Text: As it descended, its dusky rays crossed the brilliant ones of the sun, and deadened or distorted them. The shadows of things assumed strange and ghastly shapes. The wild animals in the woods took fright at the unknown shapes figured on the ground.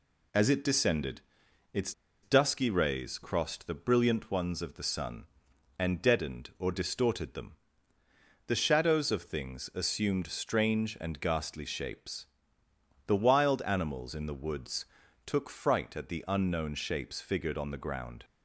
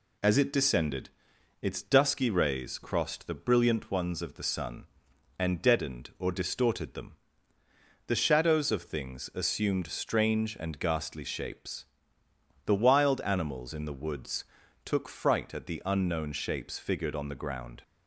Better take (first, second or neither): second